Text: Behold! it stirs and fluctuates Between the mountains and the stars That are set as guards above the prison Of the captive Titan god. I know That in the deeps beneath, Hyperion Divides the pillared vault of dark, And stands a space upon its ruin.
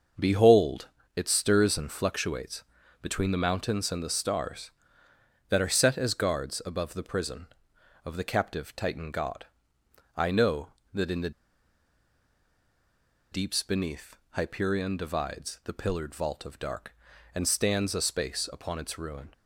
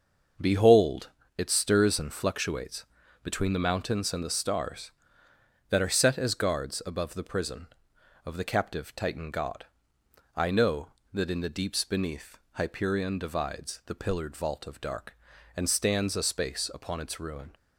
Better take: second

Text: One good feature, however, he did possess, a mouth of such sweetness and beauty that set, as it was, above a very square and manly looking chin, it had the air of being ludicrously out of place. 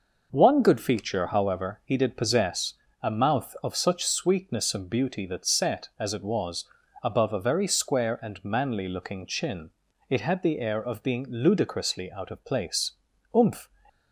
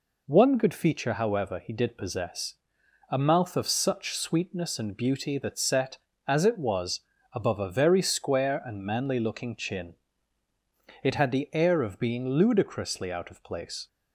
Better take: second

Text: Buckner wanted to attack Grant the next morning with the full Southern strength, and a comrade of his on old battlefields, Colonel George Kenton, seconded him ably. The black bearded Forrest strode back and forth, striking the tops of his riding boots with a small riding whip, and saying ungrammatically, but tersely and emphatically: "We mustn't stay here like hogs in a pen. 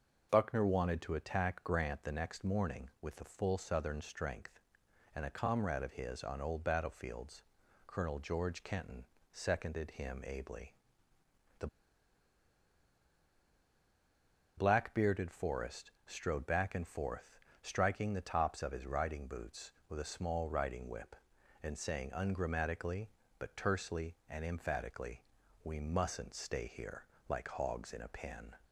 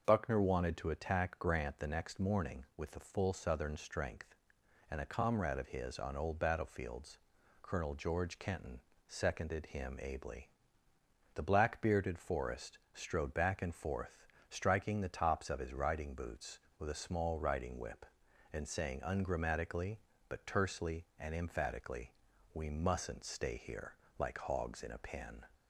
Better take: second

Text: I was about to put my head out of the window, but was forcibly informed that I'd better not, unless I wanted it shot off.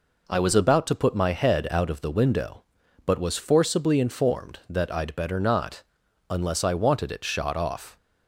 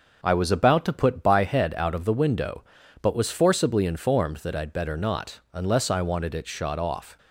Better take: first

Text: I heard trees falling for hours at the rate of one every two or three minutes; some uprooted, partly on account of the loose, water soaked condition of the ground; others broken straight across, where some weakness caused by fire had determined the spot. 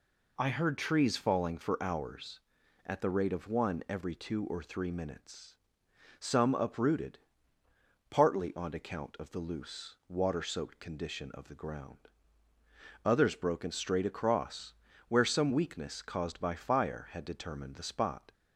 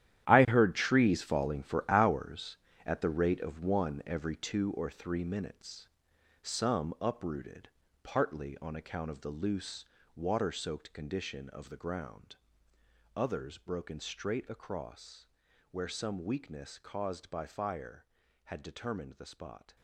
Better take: first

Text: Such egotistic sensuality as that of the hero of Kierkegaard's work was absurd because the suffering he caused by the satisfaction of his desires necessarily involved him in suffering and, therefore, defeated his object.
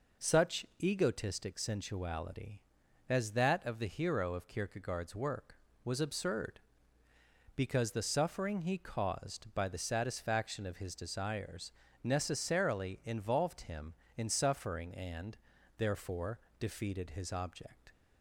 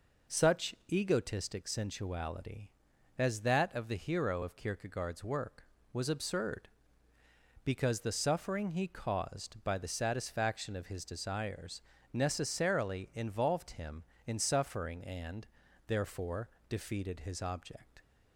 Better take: neither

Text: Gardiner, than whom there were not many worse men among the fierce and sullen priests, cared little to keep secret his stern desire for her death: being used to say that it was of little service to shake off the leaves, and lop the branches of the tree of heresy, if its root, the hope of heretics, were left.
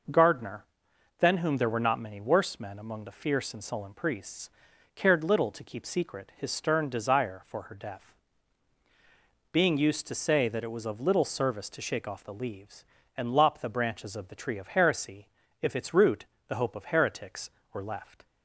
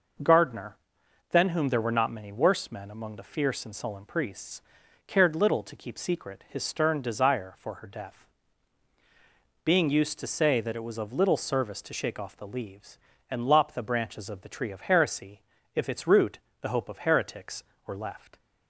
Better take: neither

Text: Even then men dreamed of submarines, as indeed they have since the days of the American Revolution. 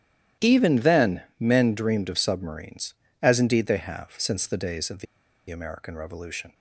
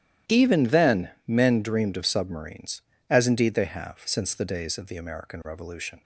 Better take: second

